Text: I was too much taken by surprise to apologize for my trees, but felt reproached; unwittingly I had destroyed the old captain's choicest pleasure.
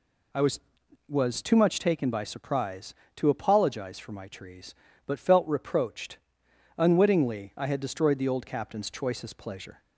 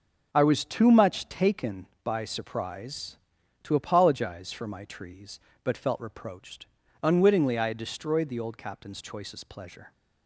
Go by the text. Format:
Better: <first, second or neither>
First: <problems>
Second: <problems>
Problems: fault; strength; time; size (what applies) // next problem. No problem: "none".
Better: second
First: says "was" twice; at 1.0 s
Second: none